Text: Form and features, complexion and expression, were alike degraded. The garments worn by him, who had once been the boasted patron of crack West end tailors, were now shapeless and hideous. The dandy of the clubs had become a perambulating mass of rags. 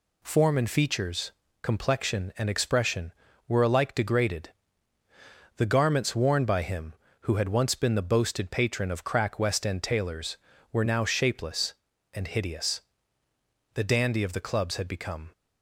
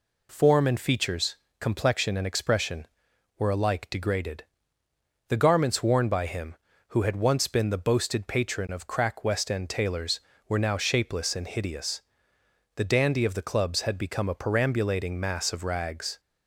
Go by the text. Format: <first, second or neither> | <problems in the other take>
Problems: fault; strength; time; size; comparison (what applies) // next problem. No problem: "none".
second | stops before "a perambulating mass of rags"; at 15.3 s